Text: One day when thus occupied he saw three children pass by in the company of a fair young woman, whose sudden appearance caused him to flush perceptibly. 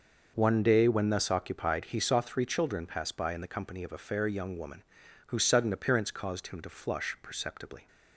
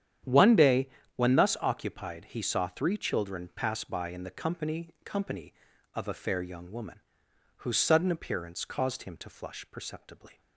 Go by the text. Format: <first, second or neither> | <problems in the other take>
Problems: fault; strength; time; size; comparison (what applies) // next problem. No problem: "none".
first | starts louder than the rest; strong; until 1.5 s; 9.5 dB // pauses between "day" and "when"; slight; at 0.8 s; 0.28 s long // says "company" twice; at 5.0 s